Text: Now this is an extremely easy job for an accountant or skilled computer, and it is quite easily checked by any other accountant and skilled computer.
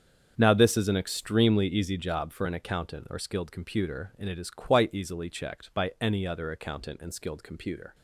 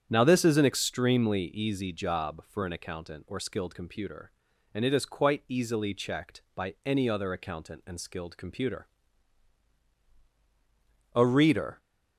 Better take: first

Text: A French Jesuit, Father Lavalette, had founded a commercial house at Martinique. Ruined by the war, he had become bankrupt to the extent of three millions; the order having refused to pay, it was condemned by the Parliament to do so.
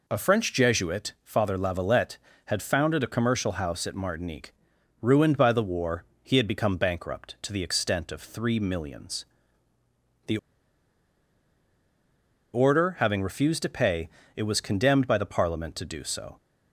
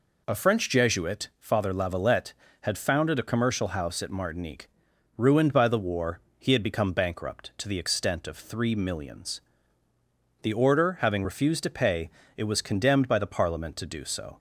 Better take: second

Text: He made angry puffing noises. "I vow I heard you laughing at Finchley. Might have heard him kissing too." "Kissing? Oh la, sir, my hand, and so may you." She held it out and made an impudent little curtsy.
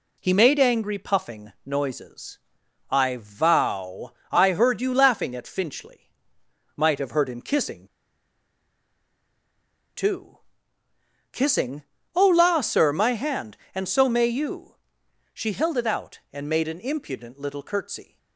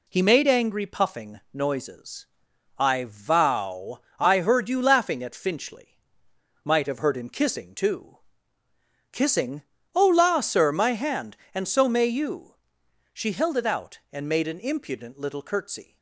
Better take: second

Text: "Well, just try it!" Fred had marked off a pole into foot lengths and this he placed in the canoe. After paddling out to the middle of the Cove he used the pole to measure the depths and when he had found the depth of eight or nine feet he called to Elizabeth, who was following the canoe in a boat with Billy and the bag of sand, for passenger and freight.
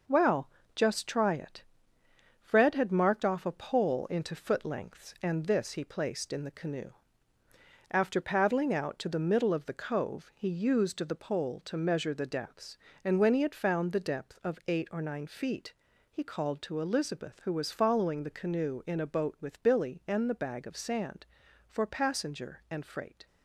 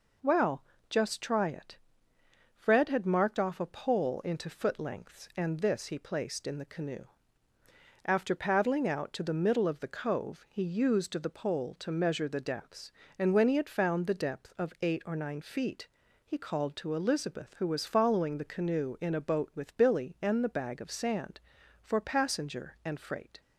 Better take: second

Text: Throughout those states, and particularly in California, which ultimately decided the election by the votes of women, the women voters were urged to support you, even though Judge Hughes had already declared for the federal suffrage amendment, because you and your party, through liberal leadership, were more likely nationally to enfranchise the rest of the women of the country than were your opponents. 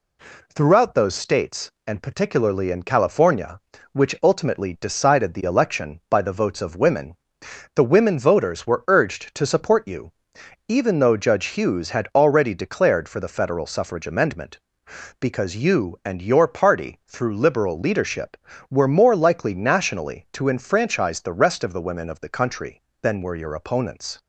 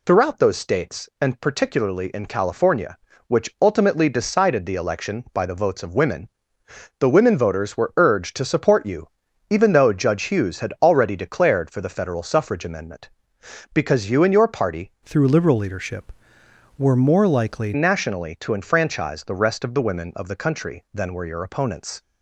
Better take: first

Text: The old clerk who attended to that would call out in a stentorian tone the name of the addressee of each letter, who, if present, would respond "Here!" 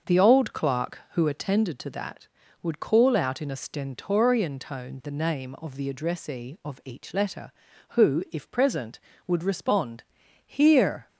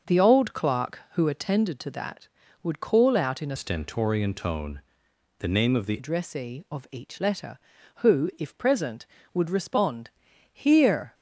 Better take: first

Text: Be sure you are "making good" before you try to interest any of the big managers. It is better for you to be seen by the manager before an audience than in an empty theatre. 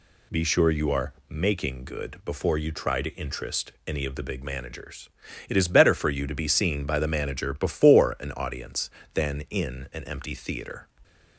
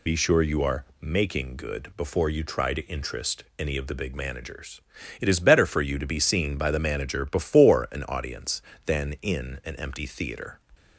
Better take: first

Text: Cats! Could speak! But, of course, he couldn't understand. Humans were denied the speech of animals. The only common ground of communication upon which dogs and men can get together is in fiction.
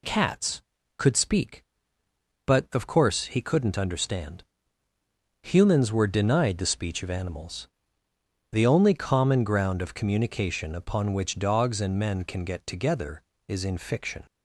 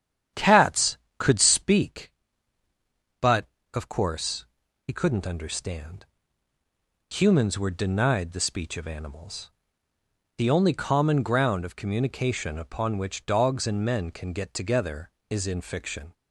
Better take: first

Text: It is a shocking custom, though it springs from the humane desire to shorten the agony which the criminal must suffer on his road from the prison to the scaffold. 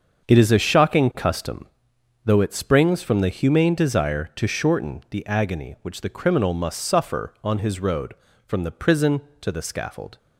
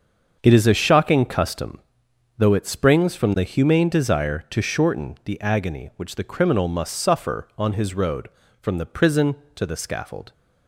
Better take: neither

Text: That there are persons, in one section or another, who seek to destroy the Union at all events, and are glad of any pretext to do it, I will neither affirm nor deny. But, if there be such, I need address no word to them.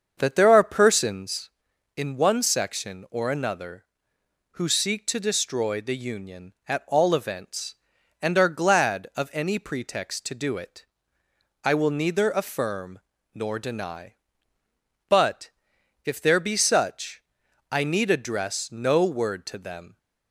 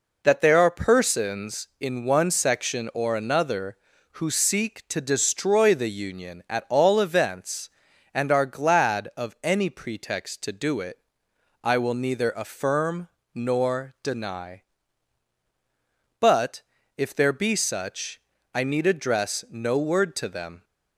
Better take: second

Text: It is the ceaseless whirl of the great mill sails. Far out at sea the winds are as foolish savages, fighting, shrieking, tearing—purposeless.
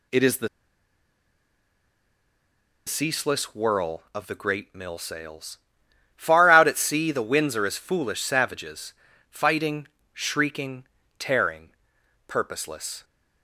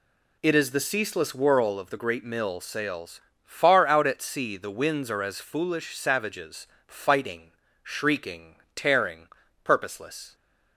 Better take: second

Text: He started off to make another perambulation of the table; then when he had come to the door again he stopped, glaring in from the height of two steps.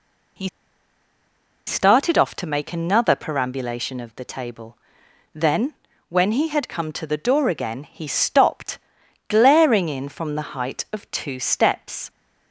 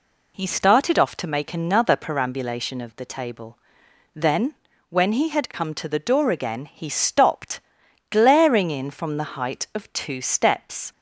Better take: second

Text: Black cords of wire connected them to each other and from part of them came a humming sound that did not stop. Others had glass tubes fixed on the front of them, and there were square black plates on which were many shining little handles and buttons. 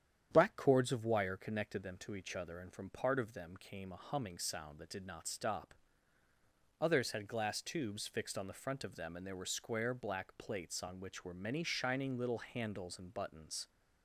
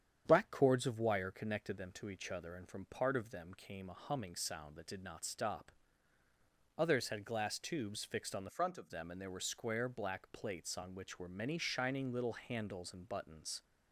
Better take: first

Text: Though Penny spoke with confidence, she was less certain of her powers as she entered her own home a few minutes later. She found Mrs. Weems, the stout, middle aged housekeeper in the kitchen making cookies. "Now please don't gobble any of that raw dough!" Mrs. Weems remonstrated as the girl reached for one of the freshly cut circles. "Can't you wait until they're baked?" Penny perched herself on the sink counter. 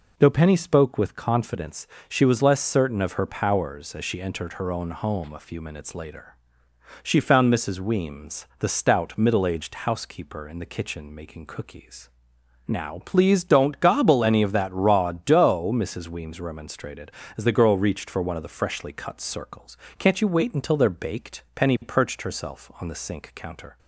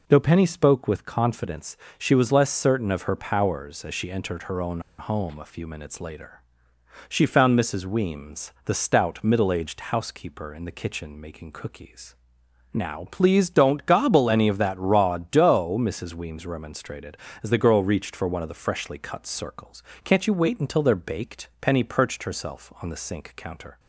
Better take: first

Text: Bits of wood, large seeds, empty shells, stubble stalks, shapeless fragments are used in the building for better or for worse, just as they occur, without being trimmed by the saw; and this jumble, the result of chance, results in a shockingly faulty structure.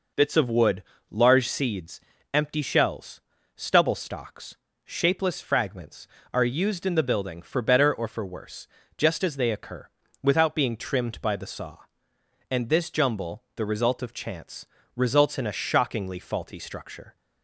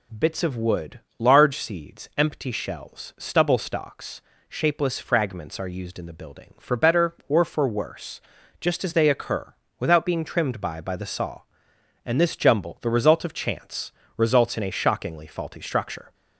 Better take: first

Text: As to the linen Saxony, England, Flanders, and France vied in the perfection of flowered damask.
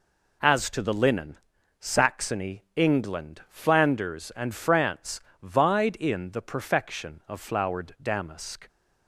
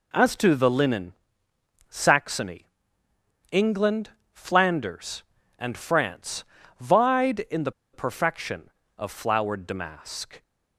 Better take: first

